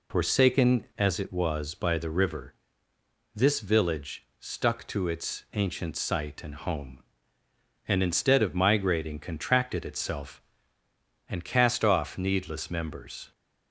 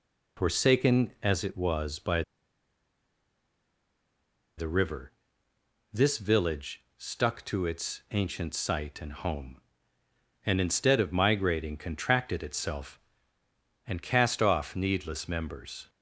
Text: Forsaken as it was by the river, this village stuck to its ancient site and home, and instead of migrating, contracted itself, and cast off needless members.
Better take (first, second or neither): first